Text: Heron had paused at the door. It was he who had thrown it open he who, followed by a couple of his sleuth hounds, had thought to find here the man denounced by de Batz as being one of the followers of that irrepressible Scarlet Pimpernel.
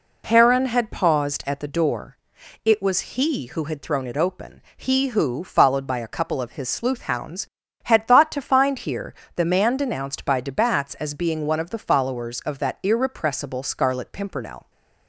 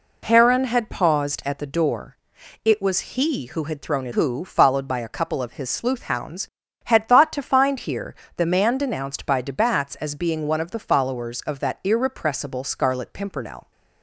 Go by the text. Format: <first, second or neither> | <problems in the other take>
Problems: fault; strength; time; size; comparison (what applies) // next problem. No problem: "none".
first | skips "open he"; at 4.1 s // pauses between "here" and "the"; slight; at 8.1 s; 0.24 s long; slight in the first